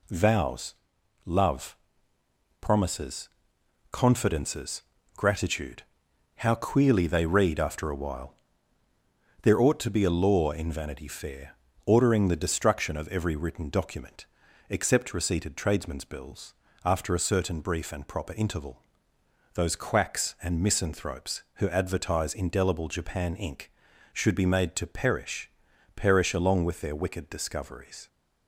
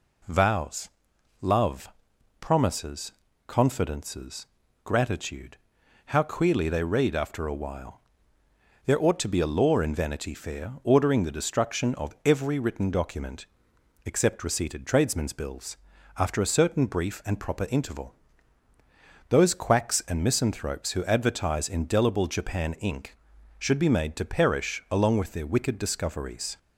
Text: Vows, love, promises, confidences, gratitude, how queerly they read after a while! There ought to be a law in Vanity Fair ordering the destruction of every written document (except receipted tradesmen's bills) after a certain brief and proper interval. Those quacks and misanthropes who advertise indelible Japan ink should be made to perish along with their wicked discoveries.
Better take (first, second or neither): second